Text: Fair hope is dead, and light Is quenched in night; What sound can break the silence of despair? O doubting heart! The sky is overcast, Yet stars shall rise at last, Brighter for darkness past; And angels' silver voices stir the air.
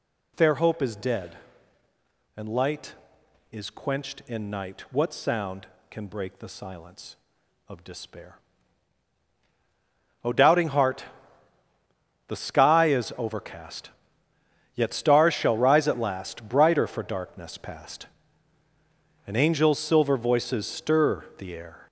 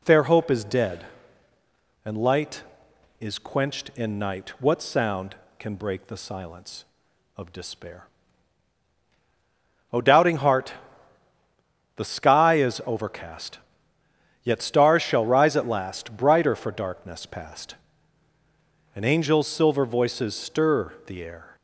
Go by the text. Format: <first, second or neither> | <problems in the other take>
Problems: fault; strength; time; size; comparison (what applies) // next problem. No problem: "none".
second | gets louder; throughout; 6 dB // pauses between "stir" and "the"; slight; at 21.2 s; 0.16 s long; slight in the second